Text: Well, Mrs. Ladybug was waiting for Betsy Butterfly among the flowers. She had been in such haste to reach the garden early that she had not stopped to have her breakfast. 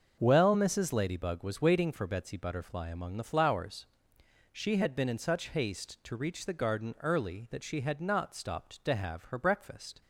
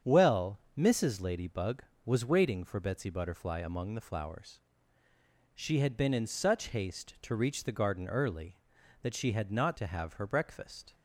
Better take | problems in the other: first | starts louder than the rest; strong; until 1.2 s; 7.5 dB; also in the first // skips "stopped"; at 9.7 s

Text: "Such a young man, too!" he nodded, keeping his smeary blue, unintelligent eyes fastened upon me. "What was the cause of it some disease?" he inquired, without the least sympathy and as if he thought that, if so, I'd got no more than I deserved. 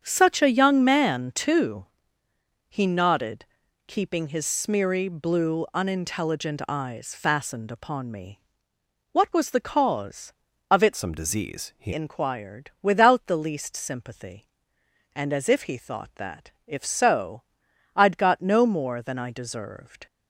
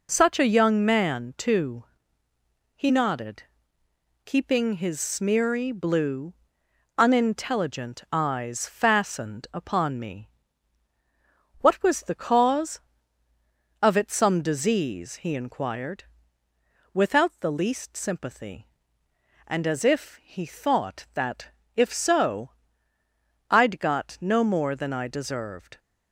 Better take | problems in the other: second | starts louder than the rest; strong; until 1.0 s; 7.5 dB // changes voice from "some" to "he"; from 10.9 to 11.9 s; 1.0 s long

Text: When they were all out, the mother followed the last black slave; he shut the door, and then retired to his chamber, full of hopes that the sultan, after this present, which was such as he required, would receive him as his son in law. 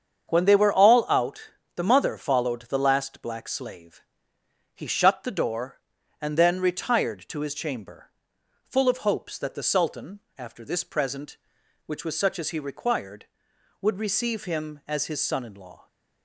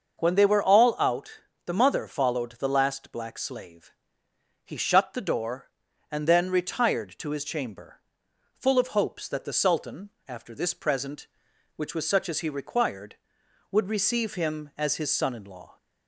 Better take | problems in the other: second | gets quieter; throughout; 7 dB // starts louder than the rest; strong; until 1.3 s; 7.5 dB; also in the second

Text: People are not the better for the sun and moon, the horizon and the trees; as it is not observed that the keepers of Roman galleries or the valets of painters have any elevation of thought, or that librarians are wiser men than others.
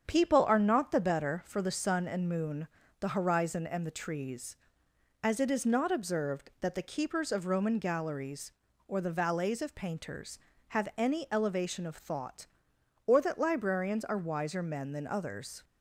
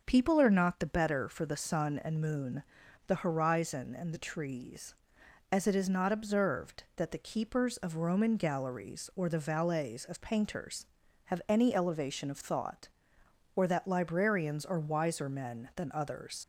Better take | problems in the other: first | starts louder than the rest; until 1.0 s; 6.5 dB; strong in the first // leaves "others" unfinished; at 16.4 s; 70 ms

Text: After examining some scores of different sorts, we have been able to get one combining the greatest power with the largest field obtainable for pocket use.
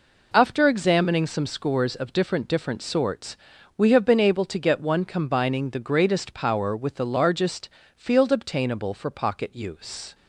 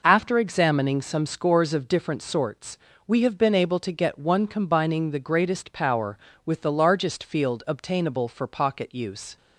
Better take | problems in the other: second | says "different" twice; at 2.4 s // pauses between "largest" and "field"; slight; at 7.6 s; 0.28 s long

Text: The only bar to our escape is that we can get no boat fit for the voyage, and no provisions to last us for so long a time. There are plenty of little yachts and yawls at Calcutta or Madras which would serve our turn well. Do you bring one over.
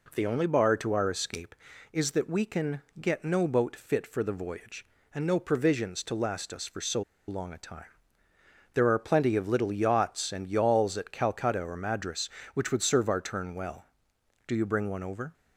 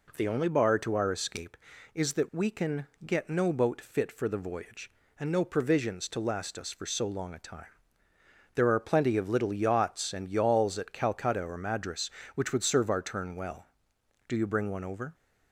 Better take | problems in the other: second | pauses between "can" and "get"; slight; at 2.8 s; 0.18 s long; slight in the second // pauses between "so" and "long"; slight; at 7.0 s; 0.26 s long

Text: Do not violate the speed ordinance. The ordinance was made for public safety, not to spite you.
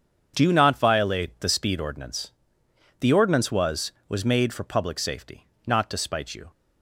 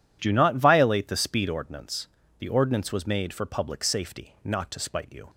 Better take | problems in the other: second | starts louder than the rest; strong; until 1.3 s; 7.5 dB // says "was" twice; at 4.0 s

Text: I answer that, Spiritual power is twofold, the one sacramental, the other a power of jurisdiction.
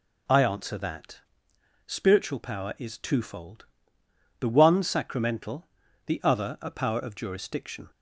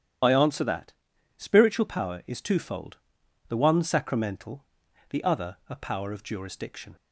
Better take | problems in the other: first | loses the start of "I"; at 0.2 s; 35 ms // starts louder than the rest; strong; until 1.6 s; 10 dB

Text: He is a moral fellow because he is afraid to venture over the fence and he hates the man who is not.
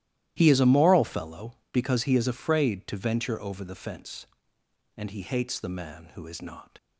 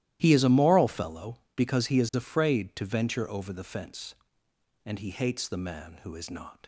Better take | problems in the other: neither | starts louder than the rest; strong; the same in both

